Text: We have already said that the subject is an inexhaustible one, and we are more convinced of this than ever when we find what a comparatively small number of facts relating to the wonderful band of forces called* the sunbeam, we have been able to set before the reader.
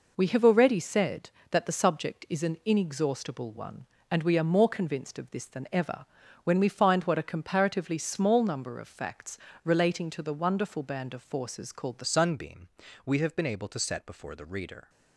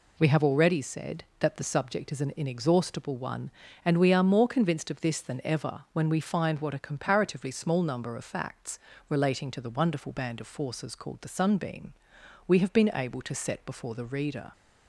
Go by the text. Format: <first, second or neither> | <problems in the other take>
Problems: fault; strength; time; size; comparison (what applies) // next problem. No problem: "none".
second | pauses between "ever" and "when"; at 6.0 s; 0.38 s long // pauses between "facts" and "relating"; slight; at 9.3 s; 0.28 s long; slight in the second // changes voice at "sunbeam"; from 12.0 s on; 2.8 s long